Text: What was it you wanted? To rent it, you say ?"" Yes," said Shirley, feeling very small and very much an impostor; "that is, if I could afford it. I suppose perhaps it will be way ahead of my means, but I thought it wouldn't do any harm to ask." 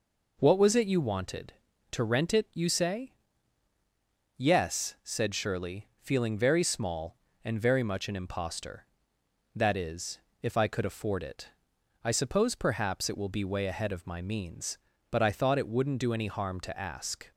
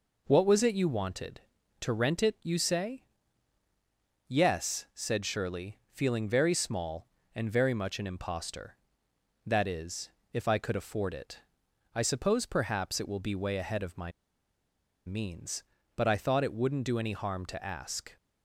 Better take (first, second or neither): first